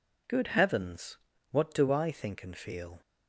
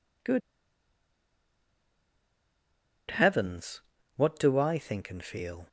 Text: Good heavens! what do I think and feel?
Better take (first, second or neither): first